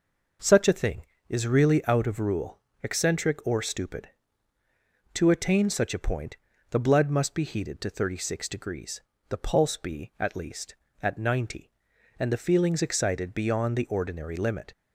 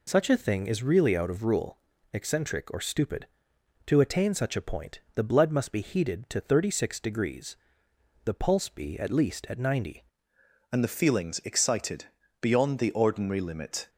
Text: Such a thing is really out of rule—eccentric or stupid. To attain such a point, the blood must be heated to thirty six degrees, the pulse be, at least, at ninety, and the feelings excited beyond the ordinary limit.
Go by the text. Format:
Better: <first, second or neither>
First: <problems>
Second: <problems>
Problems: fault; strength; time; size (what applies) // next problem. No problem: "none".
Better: first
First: none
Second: changes voice at "and"; from 10.7 s on; 3.1 s long // pauses between "excited" and "beyond"; at 12.0 s; 0.38 s long